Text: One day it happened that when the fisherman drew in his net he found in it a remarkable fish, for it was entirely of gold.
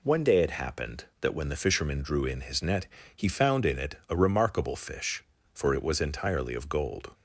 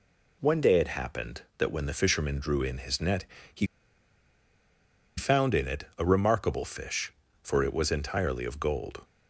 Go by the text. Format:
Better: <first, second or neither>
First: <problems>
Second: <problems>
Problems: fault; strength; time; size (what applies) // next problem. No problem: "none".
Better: first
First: pauses between "net" and "he"; slight; at 2.8 s; 0.28 s long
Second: pauses between "net" and "he"; slight; at 3.2 s; 0.28 s long // pauses between "he" and "found"; strong; at 3.6 s; 1.5 s long